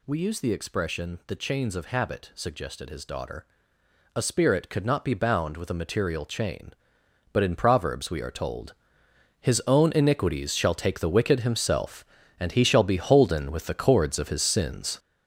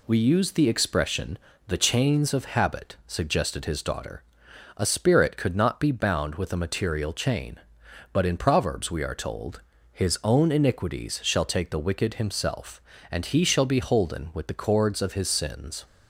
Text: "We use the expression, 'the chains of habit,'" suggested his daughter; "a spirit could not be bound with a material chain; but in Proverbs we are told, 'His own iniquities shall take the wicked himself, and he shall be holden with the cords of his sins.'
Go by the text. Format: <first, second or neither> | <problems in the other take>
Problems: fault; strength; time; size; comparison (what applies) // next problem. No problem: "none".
second | gets louder; strong; throughout; 8 dB